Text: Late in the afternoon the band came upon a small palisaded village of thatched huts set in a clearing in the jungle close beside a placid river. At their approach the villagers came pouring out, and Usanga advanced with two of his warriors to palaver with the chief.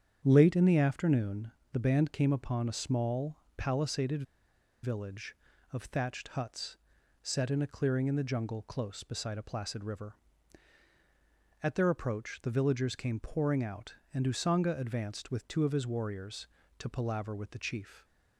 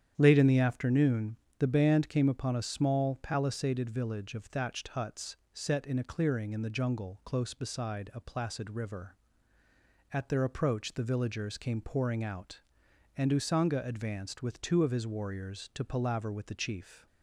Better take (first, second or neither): second